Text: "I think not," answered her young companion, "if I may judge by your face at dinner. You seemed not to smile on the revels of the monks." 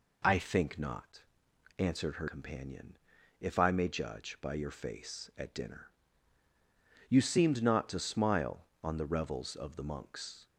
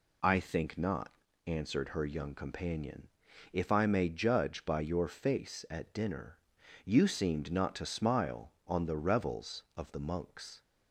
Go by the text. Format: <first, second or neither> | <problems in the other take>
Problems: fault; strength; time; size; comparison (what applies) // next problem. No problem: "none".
second | skips "young"; at 2.2 s